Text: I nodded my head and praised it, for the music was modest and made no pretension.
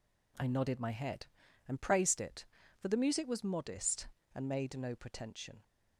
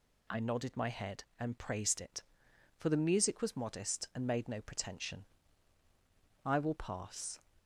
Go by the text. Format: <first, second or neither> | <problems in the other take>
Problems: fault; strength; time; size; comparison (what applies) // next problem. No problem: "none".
first | goes on to say "I will pass"; noticeable; from 6.4 s on; 0.96 s long